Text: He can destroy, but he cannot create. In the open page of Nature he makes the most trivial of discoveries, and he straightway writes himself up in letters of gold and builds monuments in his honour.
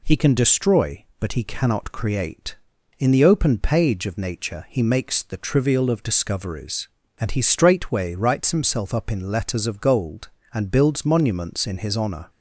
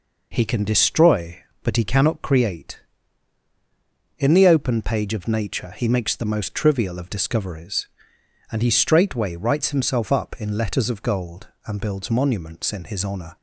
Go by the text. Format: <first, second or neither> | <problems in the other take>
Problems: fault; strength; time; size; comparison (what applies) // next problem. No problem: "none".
second | skips "most"; at 5.3 s